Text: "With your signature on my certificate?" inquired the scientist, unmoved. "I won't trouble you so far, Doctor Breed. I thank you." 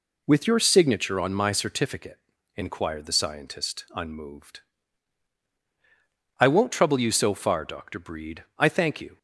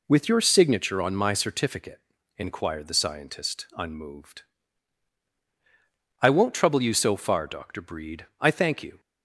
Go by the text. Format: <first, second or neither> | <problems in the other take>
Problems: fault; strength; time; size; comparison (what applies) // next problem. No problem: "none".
neither | none